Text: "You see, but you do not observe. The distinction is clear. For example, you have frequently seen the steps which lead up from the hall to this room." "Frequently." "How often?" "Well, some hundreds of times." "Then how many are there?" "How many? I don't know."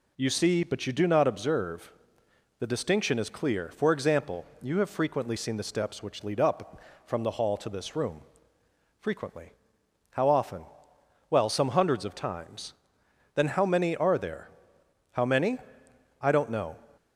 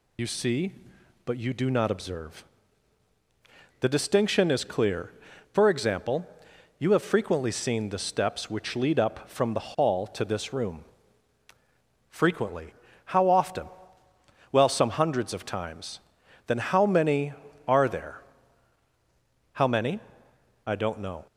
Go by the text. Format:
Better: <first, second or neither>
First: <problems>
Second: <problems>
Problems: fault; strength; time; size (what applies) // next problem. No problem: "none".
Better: first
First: none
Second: loses the start of "You"; at 0.1 s; 60 ms